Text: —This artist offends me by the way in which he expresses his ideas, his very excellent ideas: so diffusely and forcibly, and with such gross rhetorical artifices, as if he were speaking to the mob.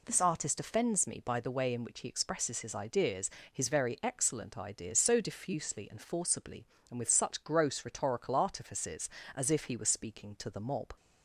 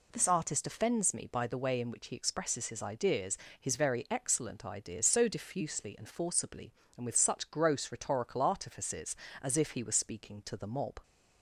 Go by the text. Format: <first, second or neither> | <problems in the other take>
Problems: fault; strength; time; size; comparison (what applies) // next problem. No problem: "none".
neither | none